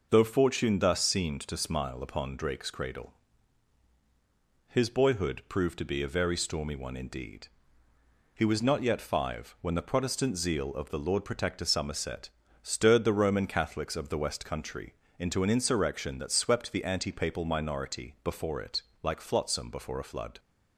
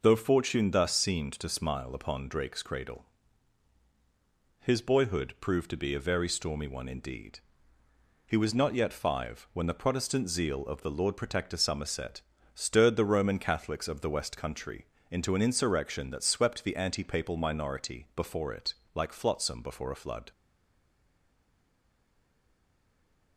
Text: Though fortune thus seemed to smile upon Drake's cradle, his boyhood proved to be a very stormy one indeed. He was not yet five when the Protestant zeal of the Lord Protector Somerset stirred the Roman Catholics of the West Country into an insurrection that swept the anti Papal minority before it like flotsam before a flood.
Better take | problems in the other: first | pauses between "Somerset" and "stirred"; slight; at 12.2 s; 0.34 s long; slight in the first // pauses between "Country" and "into"; slight; at 14.8 s; 0.24 s long; slight in the first // pauses between "it" and "like"; slight; at 18.7 s; 0.22 s long; slight in the first // stays silent after the last word; strong; from 20.3 s on; 3.0 s long

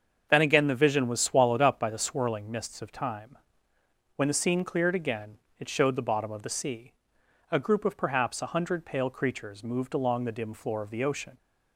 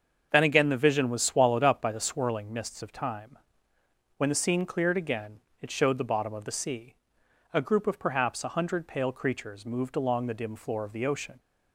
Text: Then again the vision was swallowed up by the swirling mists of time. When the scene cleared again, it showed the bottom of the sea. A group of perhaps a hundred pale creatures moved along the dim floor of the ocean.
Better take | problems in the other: neither | starts louder than the rest; the same in both

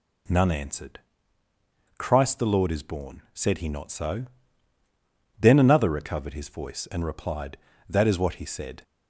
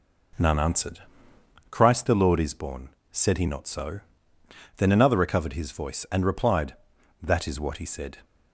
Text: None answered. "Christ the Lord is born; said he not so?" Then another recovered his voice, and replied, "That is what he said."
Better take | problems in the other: first | starts louder than the rest; noticeable; until 1.6 s; 5 dB

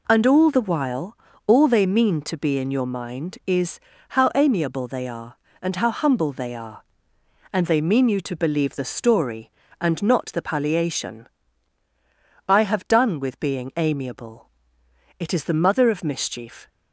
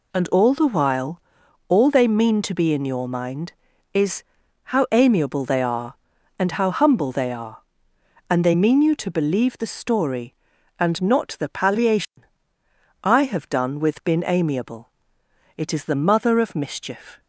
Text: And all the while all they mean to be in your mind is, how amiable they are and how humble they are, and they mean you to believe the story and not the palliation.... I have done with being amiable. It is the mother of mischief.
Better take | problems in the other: first | pauses between "while" and "all"; noticeable; at 1.2 s; 0.48 s long; slight in the first // says "been" for "being"; at 14.0 s

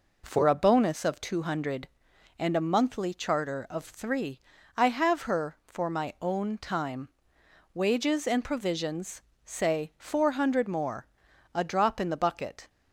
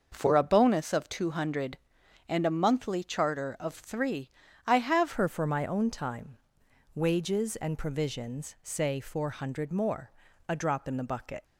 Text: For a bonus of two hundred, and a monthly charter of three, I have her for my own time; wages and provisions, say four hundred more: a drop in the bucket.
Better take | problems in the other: first | starts louder than the rest; noticeable; until 1.1 s; 6 dB // changes voice at "her"; from 5.1 s on; 6.3 s long

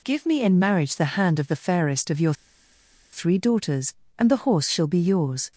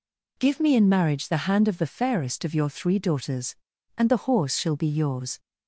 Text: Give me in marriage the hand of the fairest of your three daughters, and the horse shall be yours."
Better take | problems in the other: second | pauses between "your" and "three"; noticeable; at 2.3 s; 0.80 s long

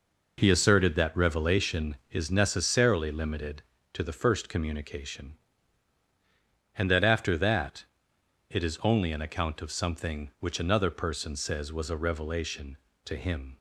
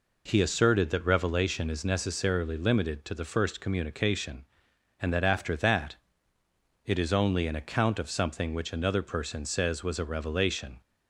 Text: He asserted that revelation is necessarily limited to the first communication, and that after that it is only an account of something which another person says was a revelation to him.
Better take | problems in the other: first | pauses between "that" and "it"; noticeable; at 5.9 s; 0.90 s long; noticeable in the first // stops before "to him"; at 10.8 s

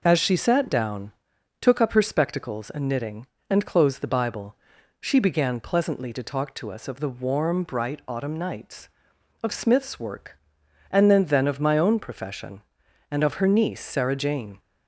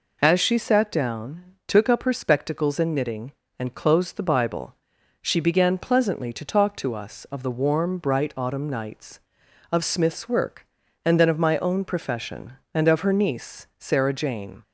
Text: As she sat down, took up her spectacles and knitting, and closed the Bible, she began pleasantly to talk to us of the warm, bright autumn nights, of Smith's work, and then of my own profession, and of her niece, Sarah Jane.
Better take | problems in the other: second | says "then" twice; at 11.2 s

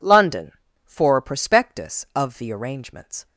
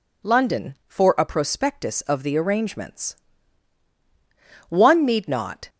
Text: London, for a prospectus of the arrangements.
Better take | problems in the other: first | goes on to say "One need not"; noticeable; from 4.6 s on; 1.0 s long

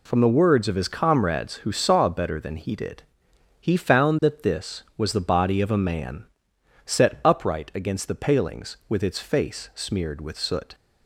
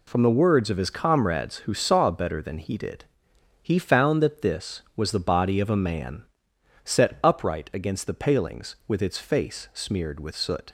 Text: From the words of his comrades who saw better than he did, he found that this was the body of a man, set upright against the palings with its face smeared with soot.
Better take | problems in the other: neither | none

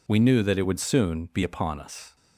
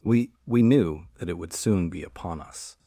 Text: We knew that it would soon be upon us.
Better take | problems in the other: first | says "We" twice; at 0.4 s

